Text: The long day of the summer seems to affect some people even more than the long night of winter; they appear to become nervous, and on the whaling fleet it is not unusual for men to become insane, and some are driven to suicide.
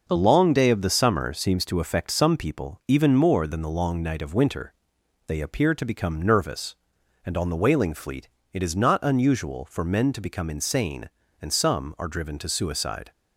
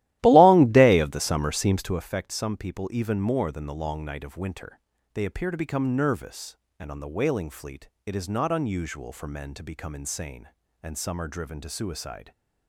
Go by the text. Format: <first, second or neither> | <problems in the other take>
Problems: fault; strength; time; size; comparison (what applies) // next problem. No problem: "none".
first | starts louder than the rest; strong; until 2.1 s; 15 dB // pauses between "fleet" and "it"; slight; at 7.8 s; 0.18 s long; slight in the first